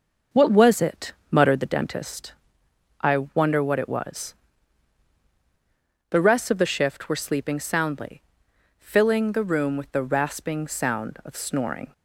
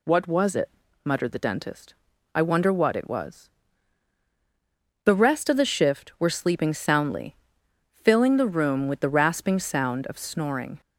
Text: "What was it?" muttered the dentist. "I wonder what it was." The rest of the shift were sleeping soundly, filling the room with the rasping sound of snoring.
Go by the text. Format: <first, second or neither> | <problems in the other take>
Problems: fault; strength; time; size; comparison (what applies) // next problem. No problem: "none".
second | starts louder than the rest; until 1.7 s; 6.5 dB